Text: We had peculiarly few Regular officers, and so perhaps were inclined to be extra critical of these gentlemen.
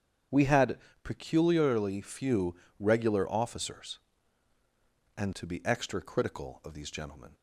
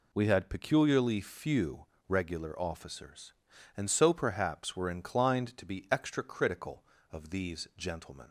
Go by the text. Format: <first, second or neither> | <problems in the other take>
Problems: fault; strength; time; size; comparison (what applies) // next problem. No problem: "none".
second | starts louder than the rest; strong; until 1.5 s; 8.5 dB // pauses between "had" and "peculiarly"; slight; at 0.7 s; 0.24 s long // pauses between "few" and "Regular"; slight; at 2.5 s; 0.24 s long; slight in the second // skips "so perhaps were inclined"; at 5.3 s